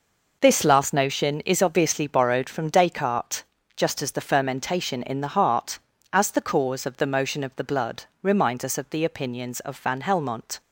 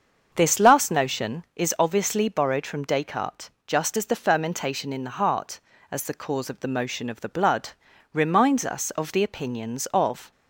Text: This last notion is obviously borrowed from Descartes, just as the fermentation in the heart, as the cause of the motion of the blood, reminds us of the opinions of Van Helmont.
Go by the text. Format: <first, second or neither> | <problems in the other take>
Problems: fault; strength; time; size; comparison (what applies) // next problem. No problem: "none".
first | starts louder than the rest; until 1.3 s; 6.5 dB // stops before "Van Helmont"; at 10.3 s